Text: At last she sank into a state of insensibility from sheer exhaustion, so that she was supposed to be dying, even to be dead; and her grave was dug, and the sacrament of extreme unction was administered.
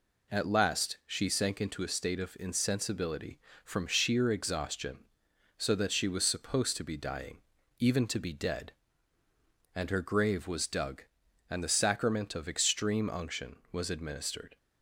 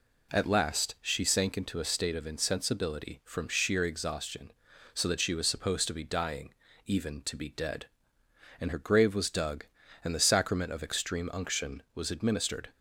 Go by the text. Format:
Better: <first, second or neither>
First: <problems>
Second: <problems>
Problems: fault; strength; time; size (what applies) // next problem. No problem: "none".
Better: neither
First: none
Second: none